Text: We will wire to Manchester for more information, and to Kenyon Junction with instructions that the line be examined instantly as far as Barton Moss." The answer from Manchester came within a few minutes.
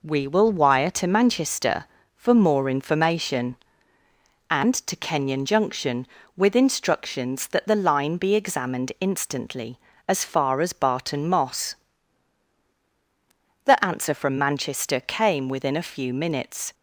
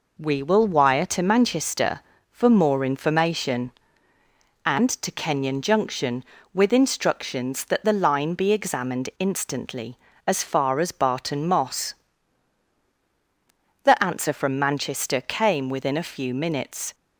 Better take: neither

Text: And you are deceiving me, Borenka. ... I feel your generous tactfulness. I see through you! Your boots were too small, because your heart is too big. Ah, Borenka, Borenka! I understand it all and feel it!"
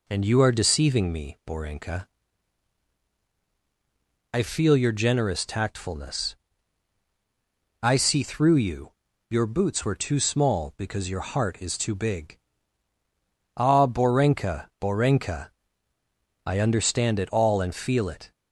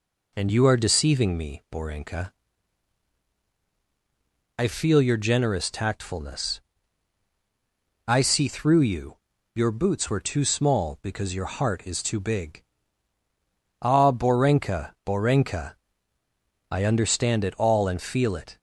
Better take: neither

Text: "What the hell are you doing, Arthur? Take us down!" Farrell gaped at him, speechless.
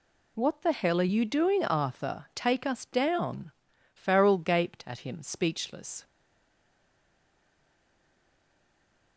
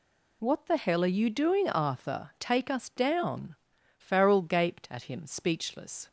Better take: second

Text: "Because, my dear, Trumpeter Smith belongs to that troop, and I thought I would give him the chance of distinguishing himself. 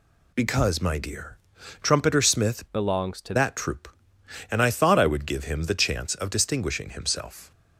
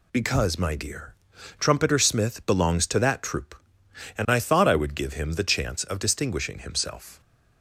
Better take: second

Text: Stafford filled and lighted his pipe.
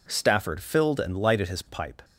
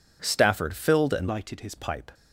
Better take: first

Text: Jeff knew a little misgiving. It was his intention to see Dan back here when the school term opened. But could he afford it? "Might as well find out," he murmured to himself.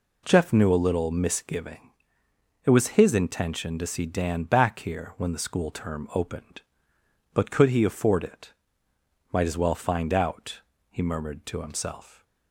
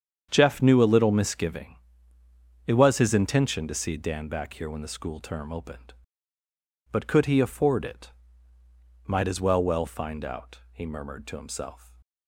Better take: first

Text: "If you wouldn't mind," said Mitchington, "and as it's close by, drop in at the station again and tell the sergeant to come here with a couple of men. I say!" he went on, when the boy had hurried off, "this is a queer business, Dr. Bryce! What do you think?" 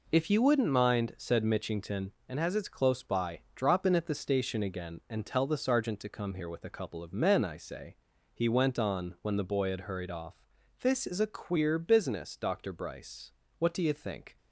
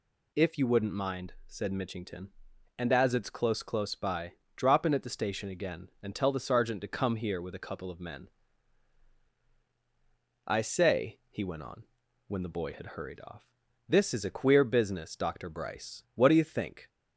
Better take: first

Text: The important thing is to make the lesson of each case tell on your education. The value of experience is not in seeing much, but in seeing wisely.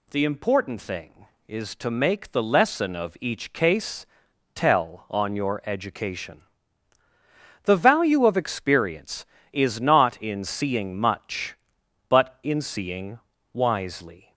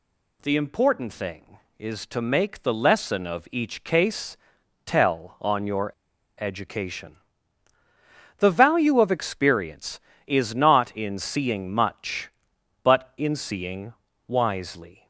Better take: first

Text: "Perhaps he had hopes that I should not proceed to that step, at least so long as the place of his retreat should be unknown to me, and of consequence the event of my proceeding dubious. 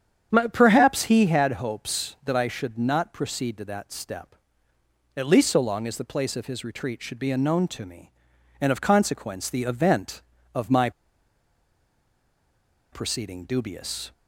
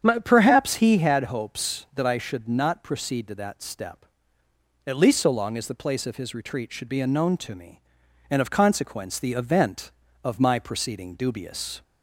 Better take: second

